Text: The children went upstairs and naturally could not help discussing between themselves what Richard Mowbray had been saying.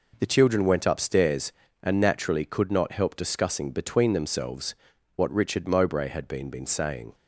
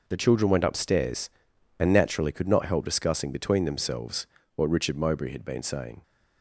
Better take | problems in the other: second | pauses between "themselves" and "what"; at 4.7 s; 0.42 s long; slight in the second // says "been" twice; at 6.5 s

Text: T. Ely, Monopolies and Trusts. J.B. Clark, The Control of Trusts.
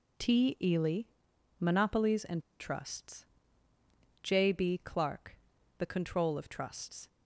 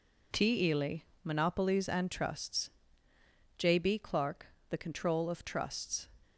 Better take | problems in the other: second | pauses between "and" and "Trusts"; slight; at 2.4 s; 0.17 s long

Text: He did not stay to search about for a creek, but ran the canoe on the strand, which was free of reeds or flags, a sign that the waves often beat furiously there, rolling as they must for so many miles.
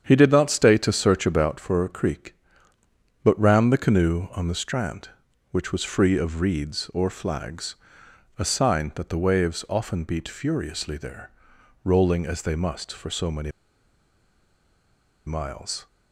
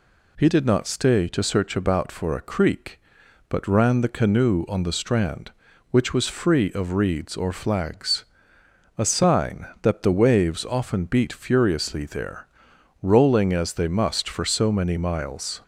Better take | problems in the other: second | starts louder than the rest; strong; until 1.0 s; 8 dB // pauses between "many" and "miles"; strong; at 13.4 s; 1.7 s long

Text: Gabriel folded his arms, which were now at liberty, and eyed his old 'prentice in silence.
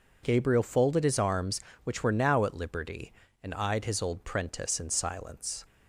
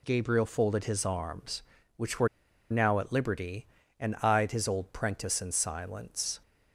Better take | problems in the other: first | pauses between "were" and "now"; at 2.2 s; 0.42 s long

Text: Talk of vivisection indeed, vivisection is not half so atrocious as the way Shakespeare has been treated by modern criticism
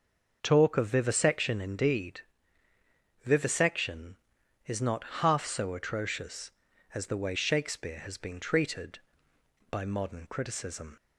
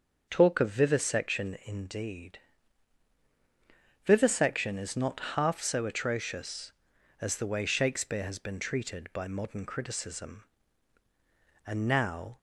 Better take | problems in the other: first | starts louder than the rest; noticeable; until 1.2 s; 6 dB; also in the first // pauses between "not" and "half"; slight; at 5.1 s; 0.16 s long; slight in the first // goes on to say "And now"; noticeable; from 11.6 s on; 0.72 s long

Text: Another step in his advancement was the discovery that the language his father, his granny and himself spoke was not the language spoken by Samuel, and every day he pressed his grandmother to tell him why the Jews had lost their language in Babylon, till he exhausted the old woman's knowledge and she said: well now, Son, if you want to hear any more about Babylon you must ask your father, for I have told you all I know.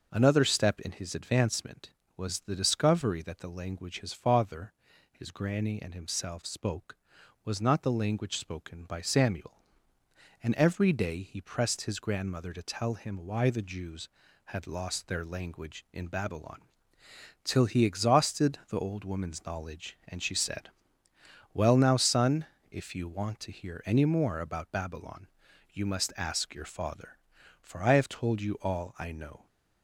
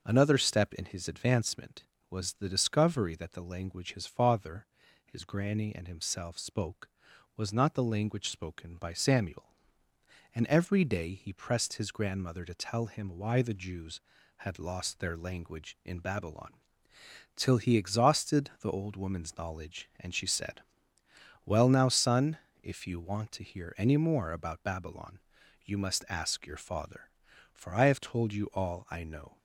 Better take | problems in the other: neither | pauses between "Babylon" and "you"; noticeable; the same in both

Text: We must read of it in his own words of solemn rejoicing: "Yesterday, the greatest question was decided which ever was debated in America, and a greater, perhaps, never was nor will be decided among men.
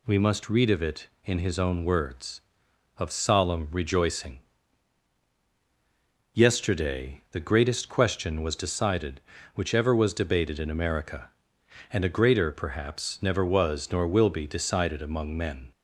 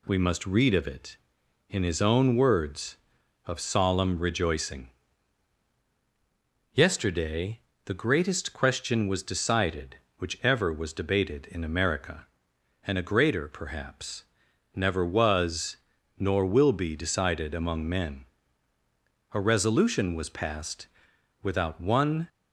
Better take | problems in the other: first | pauses between "was" and "nor"; at 15.7 s; 0.42 s long // goes on to say "A Resolution was passed without one"; strong; from 19.3 s on; 2.9 s long

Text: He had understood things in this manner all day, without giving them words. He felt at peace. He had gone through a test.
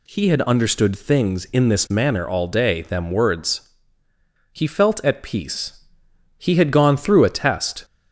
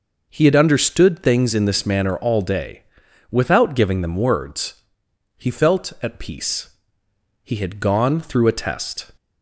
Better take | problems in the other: second | skips "without giving"; at 2.8 s

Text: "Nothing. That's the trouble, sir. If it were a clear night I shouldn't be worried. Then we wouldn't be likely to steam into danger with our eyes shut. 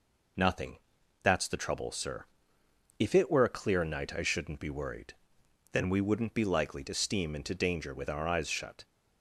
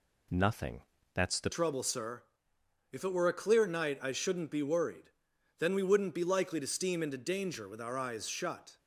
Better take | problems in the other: first | changes voice at "trouble"; from 1.5 s on; 7.2 s long

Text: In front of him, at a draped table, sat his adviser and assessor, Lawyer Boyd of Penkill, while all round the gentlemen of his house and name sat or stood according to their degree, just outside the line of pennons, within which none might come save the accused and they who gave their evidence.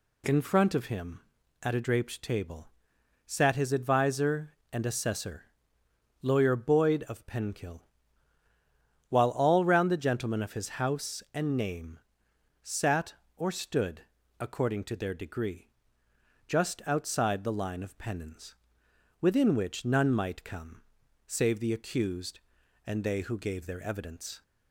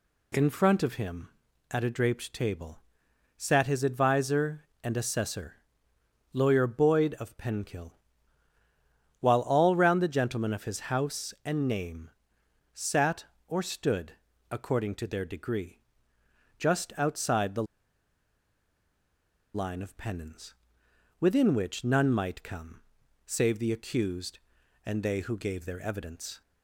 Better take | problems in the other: first | pauses between "name" and "sat"; noticeable; at 12.0 s; 0.64 s long; noticeable in the first // pauses between "stood" and "according"; slight; at 14.1 s; 0.36 s long; slight in the first // pauses between "the" and "line"; strong; at 17.6 s; 1.9 s long // pauses between "come" and "save"; at 22.8 s; 0.44 s long; also in the first

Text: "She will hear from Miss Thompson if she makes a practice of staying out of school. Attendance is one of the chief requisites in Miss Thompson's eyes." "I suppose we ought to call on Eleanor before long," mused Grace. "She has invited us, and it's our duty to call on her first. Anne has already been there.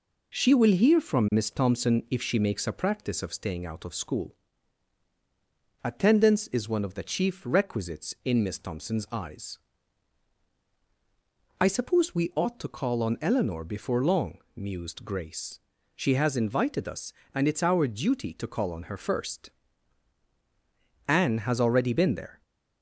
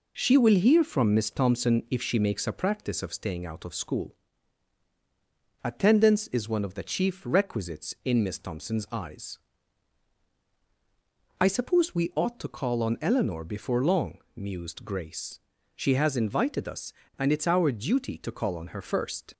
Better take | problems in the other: first | stops before "Anne has already been there"; at 19.3 s

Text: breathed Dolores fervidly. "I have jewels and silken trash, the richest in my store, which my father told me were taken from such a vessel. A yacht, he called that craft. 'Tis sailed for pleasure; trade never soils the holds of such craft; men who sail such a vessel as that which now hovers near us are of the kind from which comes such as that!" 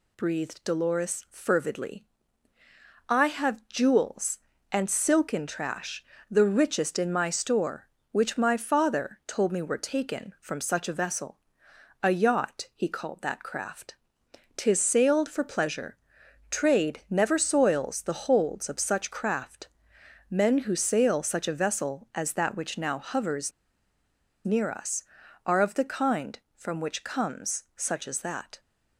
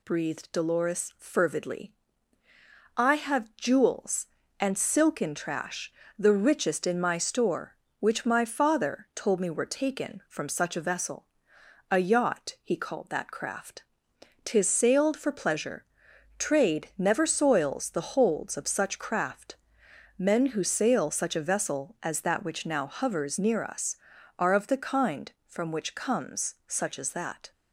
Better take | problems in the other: second | pauses between "hovers" and "near"; noticeable; at 23.5 s; 0.94 s long

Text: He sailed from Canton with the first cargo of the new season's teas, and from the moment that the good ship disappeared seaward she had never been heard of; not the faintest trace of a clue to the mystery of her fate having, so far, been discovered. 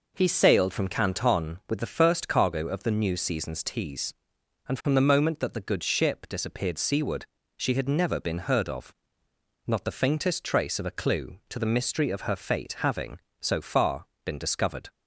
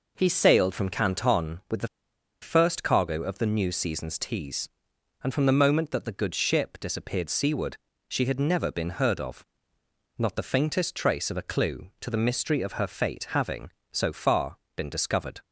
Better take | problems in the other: first | pauses between "the" and "first"; noticeable; at 1.8 s; 0.55 s long // pauses between "seaward" and "she"; slight; at 7.7 s; 0.30 s long; slight in the first

